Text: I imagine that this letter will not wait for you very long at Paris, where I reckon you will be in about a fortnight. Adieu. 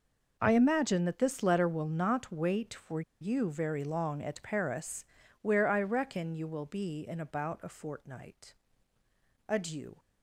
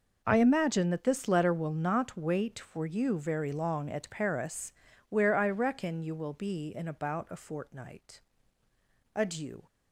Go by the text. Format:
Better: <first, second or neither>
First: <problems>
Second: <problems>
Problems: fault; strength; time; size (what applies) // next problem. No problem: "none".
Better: second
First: pauses between "for" and "you"; slight; at 3.0 s; 0.19 s long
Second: none